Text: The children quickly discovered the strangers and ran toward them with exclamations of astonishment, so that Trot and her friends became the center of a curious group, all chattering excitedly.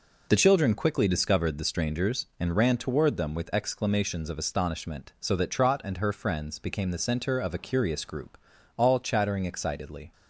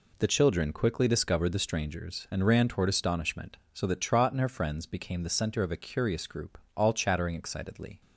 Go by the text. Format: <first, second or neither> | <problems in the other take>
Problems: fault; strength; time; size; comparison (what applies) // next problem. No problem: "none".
first | skips "them with exclamations of"; at 2.8 s